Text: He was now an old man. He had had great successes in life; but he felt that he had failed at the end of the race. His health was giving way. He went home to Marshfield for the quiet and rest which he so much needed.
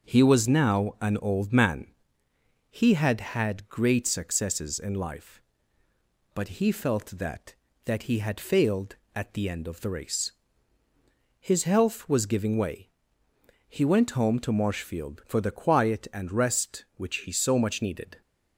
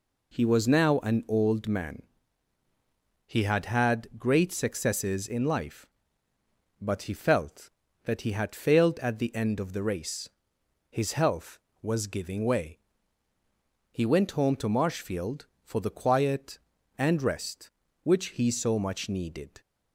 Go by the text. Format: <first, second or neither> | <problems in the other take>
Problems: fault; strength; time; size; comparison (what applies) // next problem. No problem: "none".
second | starts louder than the rest; until 1.1 s; 6.5 dB // says "that" twice; at 7.8 s